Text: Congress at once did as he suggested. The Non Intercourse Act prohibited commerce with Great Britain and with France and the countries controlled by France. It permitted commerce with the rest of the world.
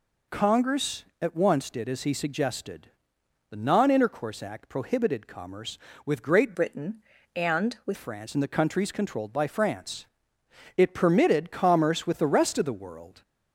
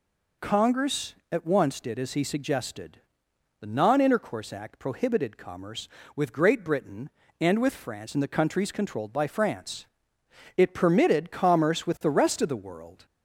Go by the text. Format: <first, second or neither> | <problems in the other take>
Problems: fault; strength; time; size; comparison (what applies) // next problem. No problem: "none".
second | changes voice from "Britain" to "with"; from 6.5 to 7.9 s; 1.4 s long